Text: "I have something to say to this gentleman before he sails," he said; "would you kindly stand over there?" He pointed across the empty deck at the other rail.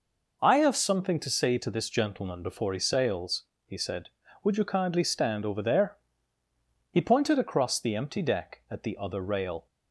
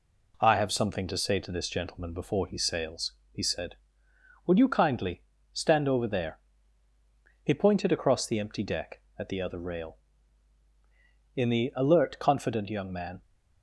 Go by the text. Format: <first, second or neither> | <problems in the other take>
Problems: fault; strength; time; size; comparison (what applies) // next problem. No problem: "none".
first | pauses between "kindly" and "stand"; slight; at 5.2 s; 0.32 s long // goes on to say "In the alert confident young man"; strong; from 11.3 s on; 1.8 s long